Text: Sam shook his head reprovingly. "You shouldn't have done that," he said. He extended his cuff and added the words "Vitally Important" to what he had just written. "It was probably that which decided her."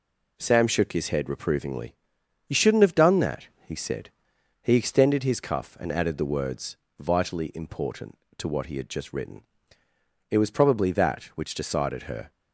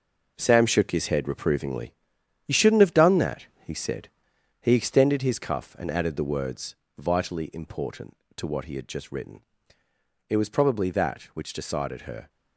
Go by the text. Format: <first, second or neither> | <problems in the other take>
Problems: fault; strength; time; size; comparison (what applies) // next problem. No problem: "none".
first | gets quieter; strong; throughout; 8.5 dB // pauses between "words" and "Vitally"; slight; at 6.7 s; 0.22 s long; slight in the first